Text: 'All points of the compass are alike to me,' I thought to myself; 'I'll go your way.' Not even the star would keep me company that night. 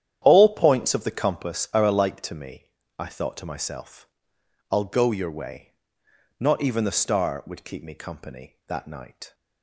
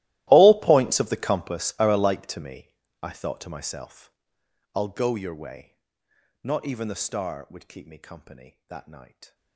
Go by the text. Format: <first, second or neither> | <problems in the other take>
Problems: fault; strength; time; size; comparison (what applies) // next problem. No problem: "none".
first | gets quieter; strong; throughout; 23 dB // starts louder than the rest; strong; until 1.3 s; 16 dB; strong in the first